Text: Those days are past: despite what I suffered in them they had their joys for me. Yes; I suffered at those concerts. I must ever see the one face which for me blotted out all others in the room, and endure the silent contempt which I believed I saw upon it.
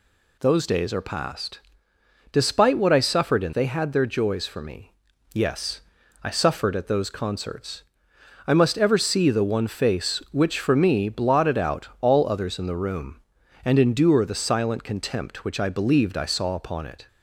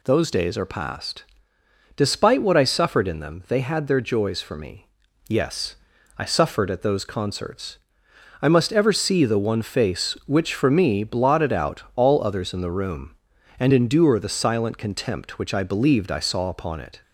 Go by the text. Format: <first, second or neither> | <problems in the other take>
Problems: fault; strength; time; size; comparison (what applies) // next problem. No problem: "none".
second | skips "them"; at 3.5 s